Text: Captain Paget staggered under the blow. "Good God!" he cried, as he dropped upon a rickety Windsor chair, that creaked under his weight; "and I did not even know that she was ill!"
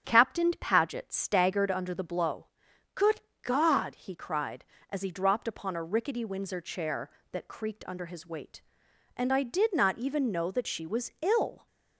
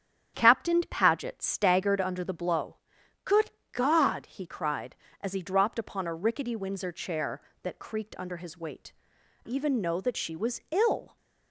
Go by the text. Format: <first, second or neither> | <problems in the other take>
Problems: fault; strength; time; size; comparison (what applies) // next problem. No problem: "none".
first | starts louder than the rest; strong; until 1.3 s; 9.5 dB; strong in the first // pauses between "Good" and "God"; slight; at 3.5 s; 0.20 s long; slight in the first // skips "and I did not"; at 9.1 s